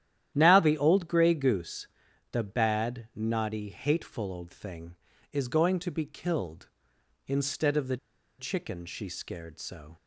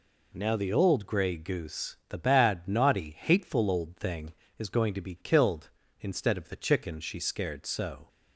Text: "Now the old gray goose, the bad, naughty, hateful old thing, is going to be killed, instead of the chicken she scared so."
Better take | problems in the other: second | starts louder than the rest; strong; until 1.3 s; 11 dB // pauses between "the" and "chicken"; at 7.9 s; 0.42 s long

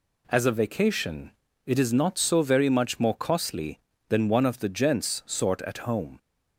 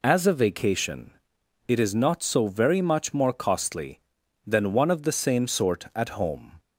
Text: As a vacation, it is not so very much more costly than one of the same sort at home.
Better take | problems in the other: second | says "gents" for "same"; at 4.6 s

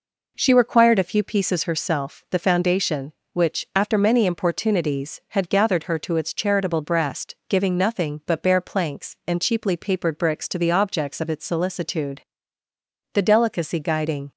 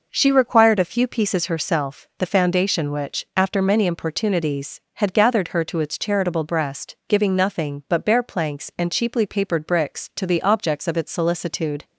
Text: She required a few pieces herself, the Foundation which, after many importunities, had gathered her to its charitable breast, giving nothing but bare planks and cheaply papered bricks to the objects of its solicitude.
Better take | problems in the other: second | goes on to say "The delicacy guiding"; noticeable; from 13.1 s on; 1.2 s long

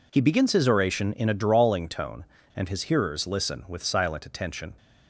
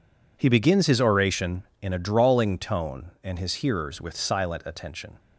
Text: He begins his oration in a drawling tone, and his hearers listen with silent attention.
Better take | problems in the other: first | skips "listen"; at 4.0 s

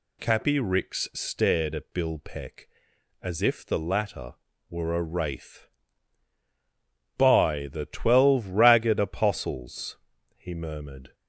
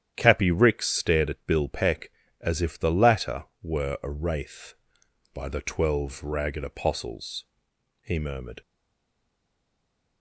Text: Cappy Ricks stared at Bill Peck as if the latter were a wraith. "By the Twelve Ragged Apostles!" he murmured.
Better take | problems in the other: first | starts louder than the rest; strong; until 1.1 s; 10 dB // stays silent after the last word; noticeable; from 8.6 s on; 1.6 s long

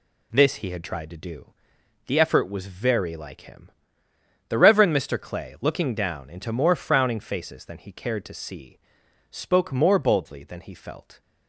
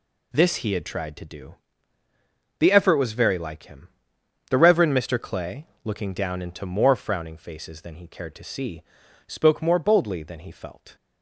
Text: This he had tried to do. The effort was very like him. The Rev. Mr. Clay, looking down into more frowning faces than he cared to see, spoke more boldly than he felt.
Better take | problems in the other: neither | none

